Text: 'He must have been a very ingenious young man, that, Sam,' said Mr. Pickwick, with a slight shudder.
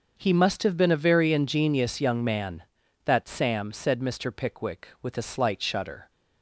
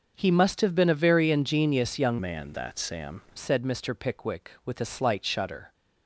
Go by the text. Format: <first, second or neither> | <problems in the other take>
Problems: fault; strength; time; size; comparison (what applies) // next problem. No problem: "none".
first | starts louder than the rest; until 1.1 s; 6.5 dB; also in the first // changes voice from "man" to "Sam"; from 2.2 to 3.2 s; 1.0 s long